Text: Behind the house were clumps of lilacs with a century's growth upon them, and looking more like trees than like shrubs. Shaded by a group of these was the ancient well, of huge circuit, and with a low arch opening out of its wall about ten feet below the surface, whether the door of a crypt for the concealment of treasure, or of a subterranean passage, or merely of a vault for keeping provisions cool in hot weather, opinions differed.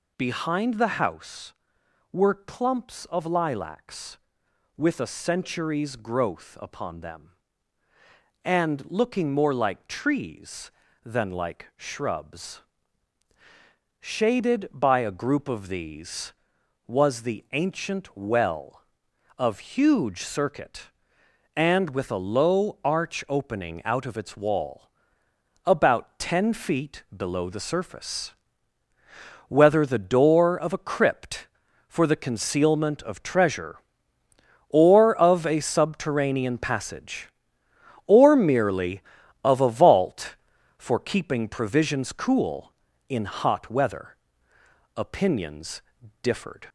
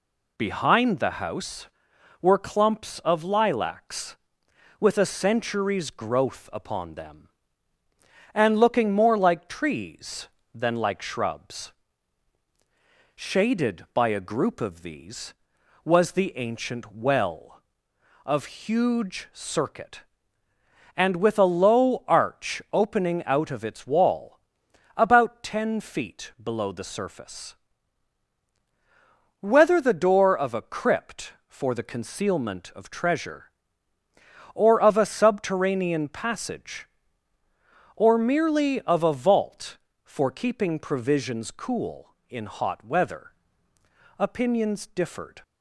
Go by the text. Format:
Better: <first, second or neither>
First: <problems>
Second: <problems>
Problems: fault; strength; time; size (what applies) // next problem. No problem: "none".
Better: second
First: gets louder; noticeable; throughout; 4 dB // pauses between "wall" and "about"; noticeable; at 24.8 s; 0.78 s long // pauses between "opinions" and "differed"; at 45.8 s; 0.40 s long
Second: pauses between "wall" and "about"; noticeable; at 24.3 s; 0.60 s long